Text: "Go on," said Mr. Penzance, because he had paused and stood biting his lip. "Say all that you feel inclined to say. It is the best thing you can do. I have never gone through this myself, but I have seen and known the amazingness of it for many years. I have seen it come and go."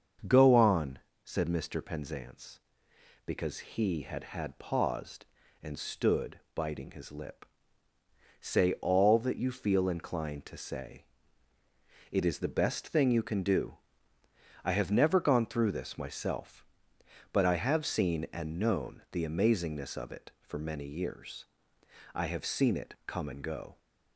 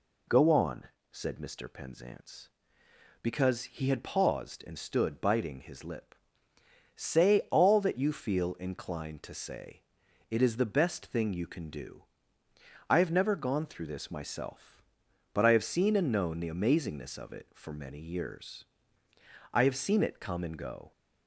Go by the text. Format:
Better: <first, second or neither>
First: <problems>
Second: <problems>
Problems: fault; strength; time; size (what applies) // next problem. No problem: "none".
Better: second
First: starts louder than the rest; until 1.5 s; 6.5 dB // says "had" twice; at 4.2 s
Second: none